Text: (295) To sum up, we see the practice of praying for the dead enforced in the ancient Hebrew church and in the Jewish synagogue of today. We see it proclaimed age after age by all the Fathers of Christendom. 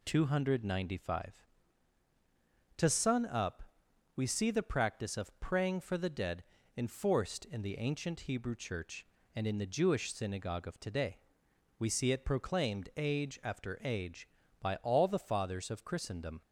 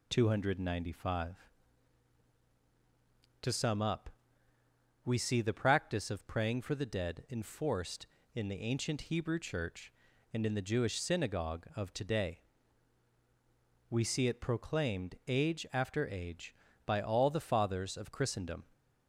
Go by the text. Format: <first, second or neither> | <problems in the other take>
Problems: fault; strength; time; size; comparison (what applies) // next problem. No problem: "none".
second | says "sun" for "sum"; at 2.8 s // pauses between "dead" and "enforced"; slight; at 6.4 s; 0.32 s long